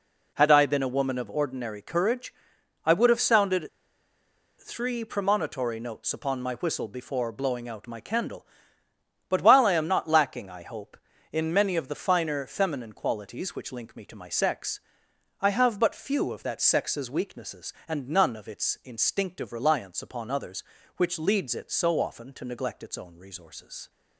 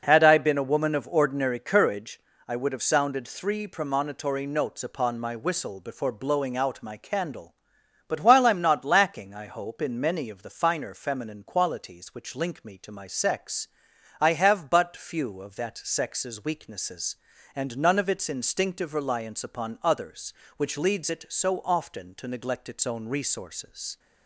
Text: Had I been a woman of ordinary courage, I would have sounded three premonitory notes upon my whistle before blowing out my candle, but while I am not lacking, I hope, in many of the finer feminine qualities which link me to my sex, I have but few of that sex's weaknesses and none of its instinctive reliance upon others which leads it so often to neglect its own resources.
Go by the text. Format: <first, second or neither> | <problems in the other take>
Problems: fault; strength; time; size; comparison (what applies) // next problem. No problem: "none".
second | pauses between "sounded" and "three"; noticeable; at 3.6 s; 0.90 s long